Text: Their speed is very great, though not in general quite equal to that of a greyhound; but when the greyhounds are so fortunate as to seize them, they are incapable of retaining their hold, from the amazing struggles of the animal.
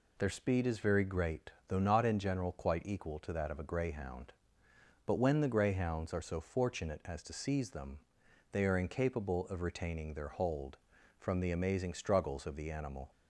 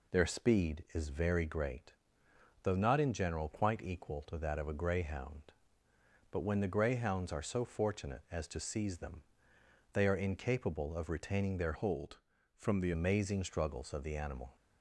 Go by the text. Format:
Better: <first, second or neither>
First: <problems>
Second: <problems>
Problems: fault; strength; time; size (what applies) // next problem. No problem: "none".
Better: first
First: none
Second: changes voice from "hold" to "the"; from 11.7 to 12.9 s; 1.2 s long